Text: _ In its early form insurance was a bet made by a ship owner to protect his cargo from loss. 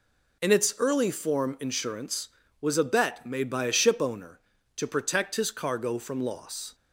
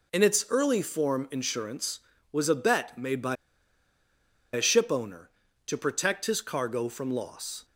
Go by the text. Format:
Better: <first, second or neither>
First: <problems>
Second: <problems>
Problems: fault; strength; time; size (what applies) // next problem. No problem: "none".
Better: first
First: none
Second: pauses between "by" and "a"; at 3.3 s; 1.1 s long